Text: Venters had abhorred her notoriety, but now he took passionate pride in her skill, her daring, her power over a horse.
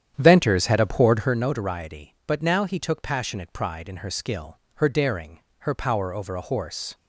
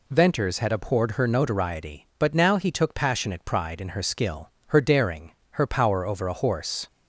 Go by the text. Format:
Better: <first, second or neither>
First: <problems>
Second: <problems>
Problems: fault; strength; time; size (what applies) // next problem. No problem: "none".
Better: second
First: starts louder than the rest; strong; until 1.4 s; 9.5 dB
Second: none